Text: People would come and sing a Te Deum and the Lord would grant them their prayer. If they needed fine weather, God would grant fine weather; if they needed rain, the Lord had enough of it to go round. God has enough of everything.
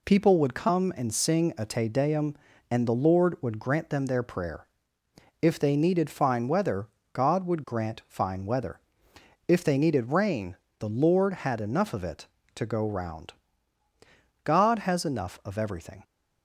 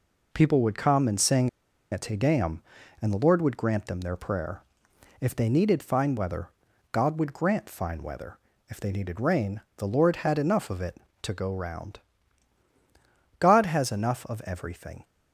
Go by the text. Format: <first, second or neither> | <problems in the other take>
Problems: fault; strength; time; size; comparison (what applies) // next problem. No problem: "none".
first | pauses between "sing" and "a"; at 1.4 s; 0.42 s long